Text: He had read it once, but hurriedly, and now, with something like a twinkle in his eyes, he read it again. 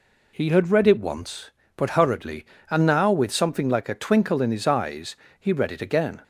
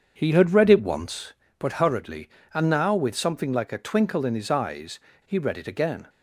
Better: first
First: none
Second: starts louder than the rest; strong; until 1.6 s; 7 dB

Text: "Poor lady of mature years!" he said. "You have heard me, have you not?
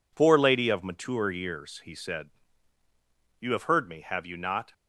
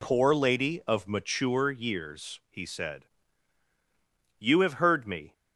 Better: first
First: none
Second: stops before "have you not"; at 5.3 s

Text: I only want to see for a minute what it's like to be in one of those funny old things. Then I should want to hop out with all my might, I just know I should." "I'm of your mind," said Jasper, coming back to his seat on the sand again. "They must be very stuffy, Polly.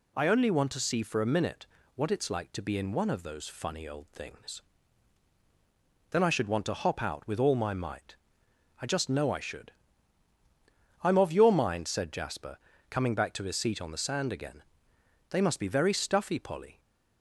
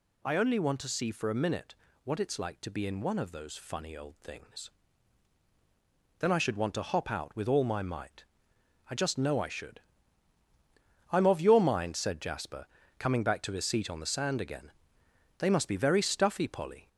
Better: first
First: pauses between "minute" and "what"; slight; at 1.6 s; 0.30 s long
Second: gets louder; throughout; 3.5 dB // pauses between "minute" and "what"; slight; at 1.7 s; 0.30 s long

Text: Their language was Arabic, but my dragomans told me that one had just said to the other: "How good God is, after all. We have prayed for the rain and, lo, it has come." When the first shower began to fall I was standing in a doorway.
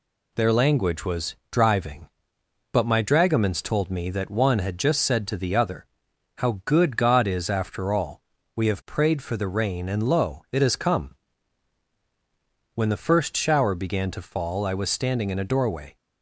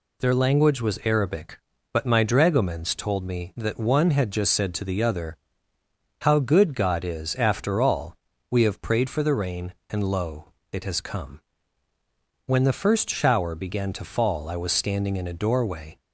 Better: second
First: says "Driving" for "Arabic"; at 1.5 s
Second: none

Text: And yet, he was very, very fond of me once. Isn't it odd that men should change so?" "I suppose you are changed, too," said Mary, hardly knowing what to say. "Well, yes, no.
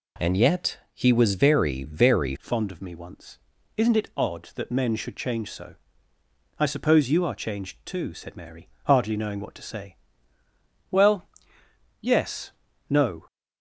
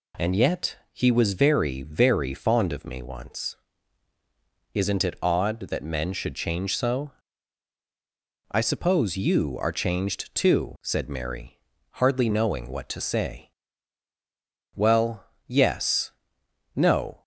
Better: second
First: changes voice at "fond"; from 2.3 s on; 10.9 s long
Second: none

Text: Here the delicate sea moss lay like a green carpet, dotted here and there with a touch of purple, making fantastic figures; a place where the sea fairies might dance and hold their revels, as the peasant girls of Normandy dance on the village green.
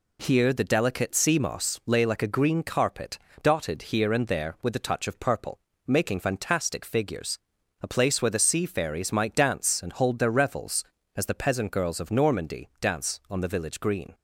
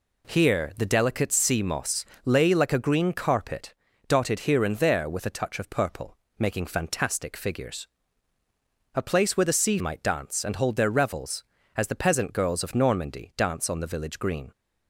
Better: first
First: none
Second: pauses between "moss" and "lay"; slight; at 2.0 s; 0.20 s long // skips "fairies"; at 9.7 s

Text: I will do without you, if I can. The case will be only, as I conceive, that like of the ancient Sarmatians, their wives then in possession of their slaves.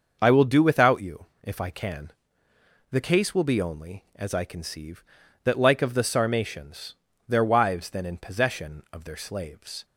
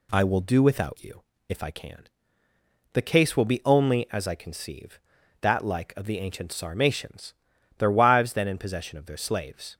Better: second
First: starts louder than the rest; until 1.2 s; 6 dB // skips "ancient"; at 6.0 s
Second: none

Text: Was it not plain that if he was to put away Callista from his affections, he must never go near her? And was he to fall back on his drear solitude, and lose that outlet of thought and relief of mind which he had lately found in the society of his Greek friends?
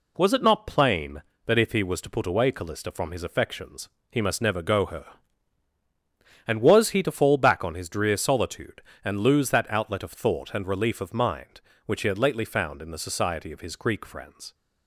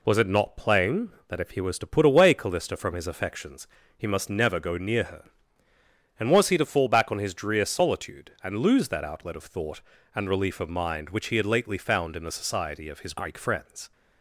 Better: second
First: skips "near"; at 4.8 s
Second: none

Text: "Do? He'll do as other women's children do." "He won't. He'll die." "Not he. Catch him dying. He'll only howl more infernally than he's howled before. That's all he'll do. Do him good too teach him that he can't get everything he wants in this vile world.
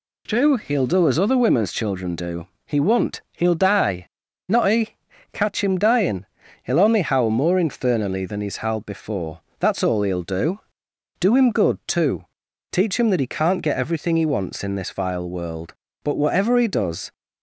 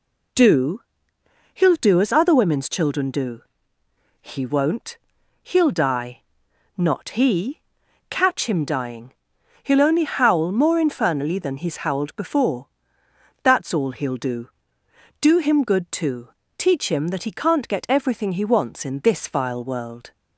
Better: second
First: pauses between "too" and "teach"; noticeable; at 12.2 s; 0.48 s long // goes on to say "But whatever he does"; noticeable; from 16.0 s on; 1.0 s long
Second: pauses between "too" and "teach"; slight; at 16.2 s; 0.28 s long

